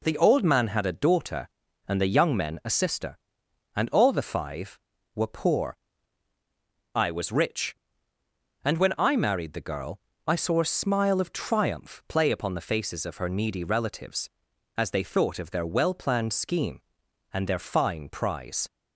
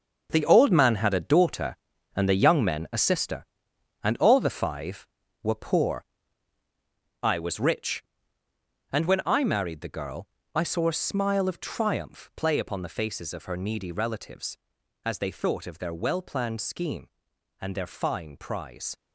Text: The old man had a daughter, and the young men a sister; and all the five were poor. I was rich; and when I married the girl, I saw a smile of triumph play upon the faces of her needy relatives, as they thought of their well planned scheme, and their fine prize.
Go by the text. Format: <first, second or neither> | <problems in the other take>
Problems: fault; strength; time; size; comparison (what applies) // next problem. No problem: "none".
first | gets quieter; strong; throughout; 10.5 dB